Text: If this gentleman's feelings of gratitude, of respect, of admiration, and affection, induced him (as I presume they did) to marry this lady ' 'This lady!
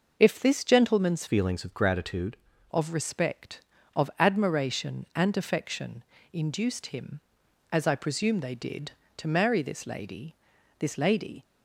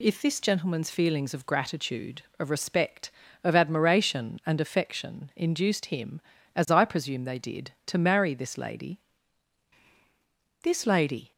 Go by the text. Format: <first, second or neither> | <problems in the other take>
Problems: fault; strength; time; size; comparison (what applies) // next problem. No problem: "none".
second | changes voice from "feelings" to "gratitude"; from 1.2 to 2.3 s; 1.1 s long